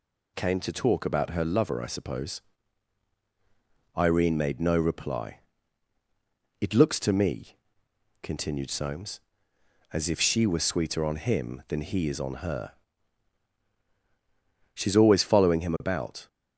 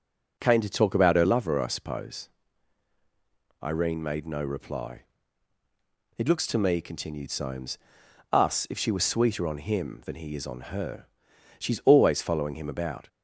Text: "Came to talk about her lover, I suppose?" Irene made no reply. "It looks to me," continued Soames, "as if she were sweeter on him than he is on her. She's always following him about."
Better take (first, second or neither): first